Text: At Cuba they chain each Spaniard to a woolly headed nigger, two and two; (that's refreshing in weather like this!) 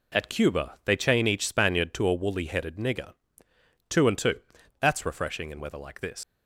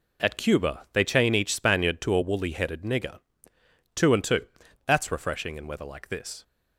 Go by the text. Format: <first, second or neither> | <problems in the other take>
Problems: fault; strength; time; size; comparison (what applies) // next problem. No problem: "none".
second | leaves "this" unfinished; at 6.2 s; 110 ms